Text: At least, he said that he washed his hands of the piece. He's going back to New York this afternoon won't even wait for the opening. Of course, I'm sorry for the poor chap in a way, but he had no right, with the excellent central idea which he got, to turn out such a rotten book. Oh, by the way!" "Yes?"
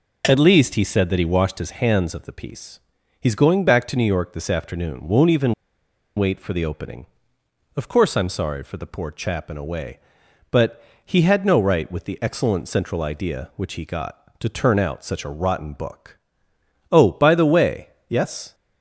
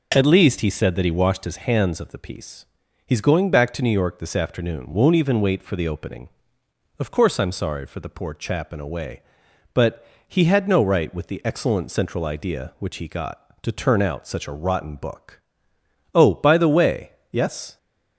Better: second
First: pauses between "even" and "wait"; noticeable; at 5.5 s; 0.64 s long // pauses between "but" and "he"; slight; at 10.8 s; 0.22 s long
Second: pauses between "but" and "he"; slight; at 10.0 s; 0.22 s long

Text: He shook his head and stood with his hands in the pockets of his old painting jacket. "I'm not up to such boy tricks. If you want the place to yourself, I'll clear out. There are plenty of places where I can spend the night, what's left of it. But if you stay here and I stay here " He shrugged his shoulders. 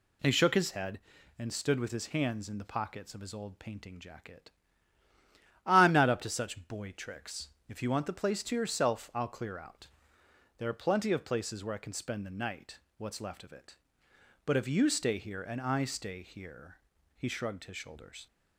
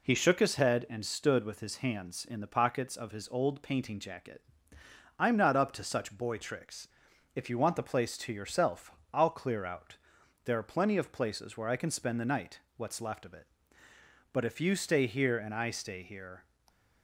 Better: first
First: none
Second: stops before "He shrugged his shoulders"; at 16.6 s

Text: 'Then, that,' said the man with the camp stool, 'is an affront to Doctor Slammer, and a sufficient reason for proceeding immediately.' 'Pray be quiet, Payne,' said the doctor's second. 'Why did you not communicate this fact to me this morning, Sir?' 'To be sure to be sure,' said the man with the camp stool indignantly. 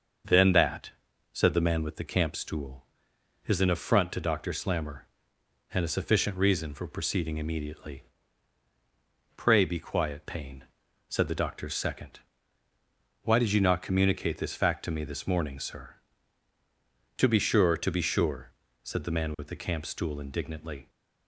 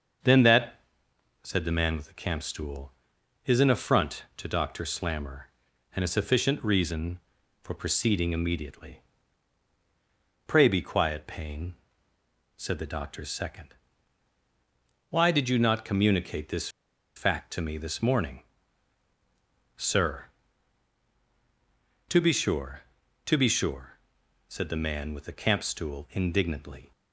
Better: first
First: starts louder than the rest; until 1.6 s; 6.5 dB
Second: starts louder than the rest; until 1.8 s; 6.5 dB // pauses between "this" and "fact"; noticeable; at 16.6 s; 0.47 s long

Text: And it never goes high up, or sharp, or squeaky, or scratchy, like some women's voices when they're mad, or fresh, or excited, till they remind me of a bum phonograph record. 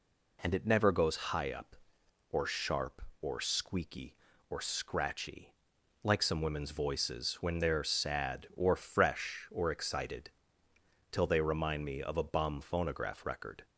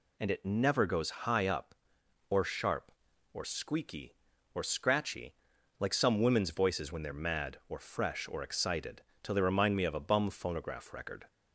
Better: second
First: says "sad" for "mad"; at 7.8 s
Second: none

